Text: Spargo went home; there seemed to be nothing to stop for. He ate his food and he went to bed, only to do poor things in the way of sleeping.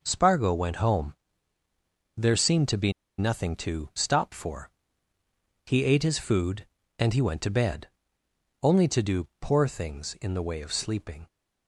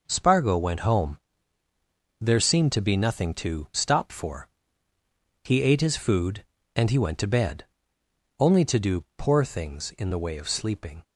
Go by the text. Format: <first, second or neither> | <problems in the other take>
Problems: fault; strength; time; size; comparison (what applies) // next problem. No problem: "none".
second | pauses between "be" and "nothing"; slight; at 2.9 s; 0.26 s long